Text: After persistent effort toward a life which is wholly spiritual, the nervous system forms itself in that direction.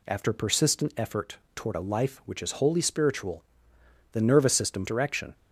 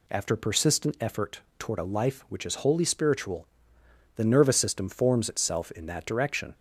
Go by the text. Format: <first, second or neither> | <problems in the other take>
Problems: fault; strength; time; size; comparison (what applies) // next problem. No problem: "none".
second | pauses between "effort" and "toward"; slight; at 1.3 s; 0.18 s long; slight in the second // skips "forms itself in that"; at 4.8 s